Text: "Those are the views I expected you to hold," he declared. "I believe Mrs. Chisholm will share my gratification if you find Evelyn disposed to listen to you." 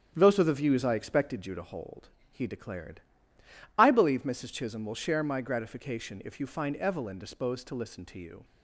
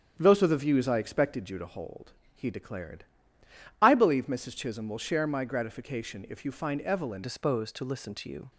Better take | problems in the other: first | starts louder than the rest; strong; until 1.2 s; 8.5 dB; strong in the first // changes voice at "disposed"; from 7.2 s on; 1.3 s long

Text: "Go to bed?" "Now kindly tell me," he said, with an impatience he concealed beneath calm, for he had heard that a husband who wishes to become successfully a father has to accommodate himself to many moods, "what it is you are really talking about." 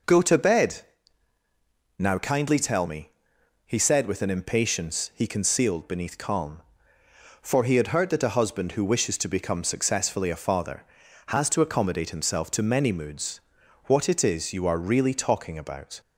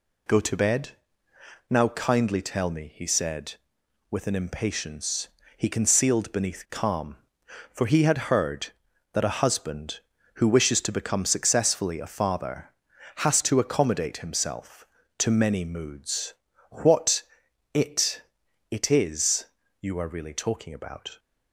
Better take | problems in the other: first | pauses between "impatience" and "he"; slight; at 5.2 s; 0.26 s long // pauses between "what" and "it"; noticeable; at 17.2 s; 0.50 s long // says "it" twice; at 18.7 s // pauses between "is" and "you"; slight; at 19.4 s; 0.34 s long

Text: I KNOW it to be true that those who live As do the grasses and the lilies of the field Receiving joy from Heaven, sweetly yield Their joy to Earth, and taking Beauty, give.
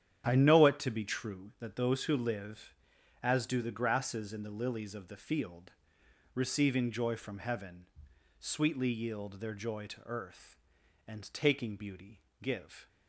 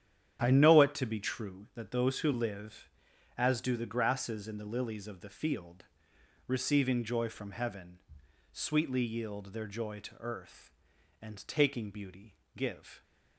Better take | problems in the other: neither | starts louder than the rest; strong; the same in both // pauses between "field" and "Receiving"; noticeable; the same in both

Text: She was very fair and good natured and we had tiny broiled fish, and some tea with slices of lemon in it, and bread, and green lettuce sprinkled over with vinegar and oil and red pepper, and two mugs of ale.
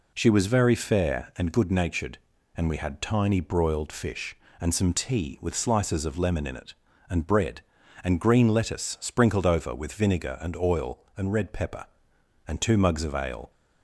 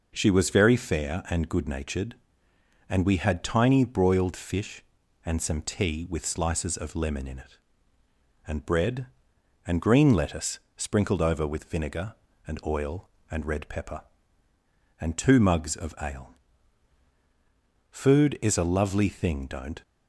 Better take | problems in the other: first | pauses between "lettuce" and "sprinkled"; slight; at 10.5 s; 0.16 s long // goes on to say "Food is a lovely thing don't"; strong; from 17.8 s on; 1.9 s long

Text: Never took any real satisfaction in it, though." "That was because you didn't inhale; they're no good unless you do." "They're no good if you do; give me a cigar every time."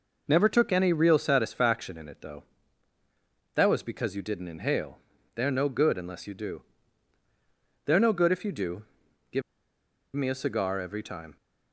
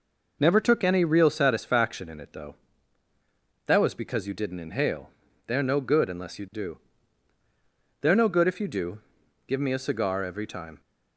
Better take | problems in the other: second | pauses between "give" and "me"; noticeable; at 9.4 s; 0.74 s long

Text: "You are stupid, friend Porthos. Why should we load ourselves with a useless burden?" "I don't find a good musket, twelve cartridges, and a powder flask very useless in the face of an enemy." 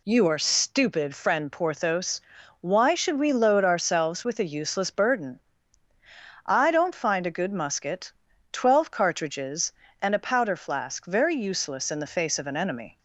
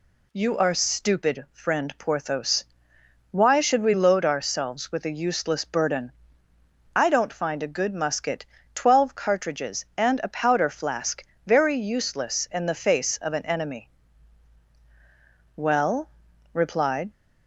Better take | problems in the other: first | pauses between "flask" and "very"; slight; at 11.2 s; 0.22 s long // goes on to say "Well replied"; from 15.5 s on; 1.5 s long

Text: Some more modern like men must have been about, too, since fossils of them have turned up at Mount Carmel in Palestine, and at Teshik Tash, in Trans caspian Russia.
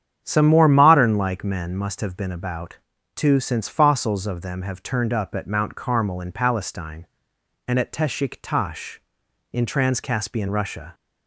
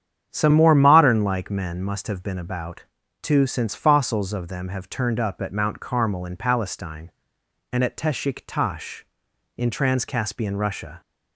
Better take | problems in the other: neither | starts louder than the rest; strong; the same in both

